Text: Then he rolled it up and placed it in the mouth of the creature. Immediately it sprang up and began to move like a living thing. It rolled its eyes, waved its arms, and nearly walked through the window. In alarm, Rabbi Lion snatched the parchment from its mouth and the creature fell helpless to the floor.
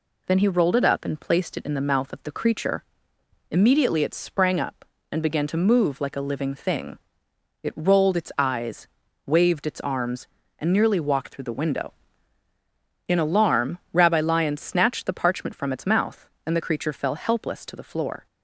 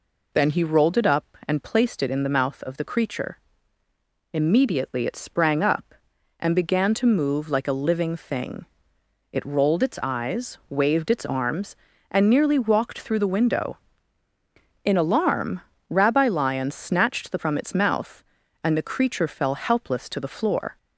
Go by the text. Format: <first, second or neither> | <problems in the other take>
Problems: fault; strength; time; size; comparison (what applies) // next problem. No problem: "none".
first | skips "parchment"; at 17.3 s